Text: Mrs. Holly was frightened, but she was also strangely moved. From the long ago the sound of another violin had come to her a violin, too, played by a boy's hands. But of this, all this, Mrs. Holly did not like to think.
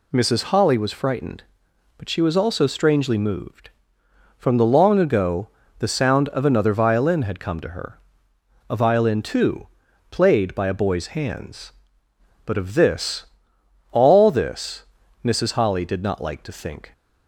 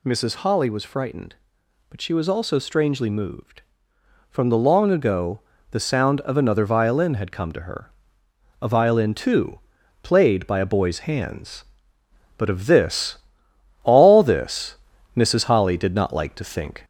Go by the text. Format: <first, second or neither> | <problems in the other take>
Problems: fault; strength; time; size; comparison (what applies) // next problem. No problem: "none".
first | gets louder; slight; throughout; 2 dB // pauses between "ago" and "the"; slight; at 5.3 s; 0.32 s long; slight in the first // pauses between "her" and "a"; noticeable; at 7.8 s; 0.72 s long; noticeable in the first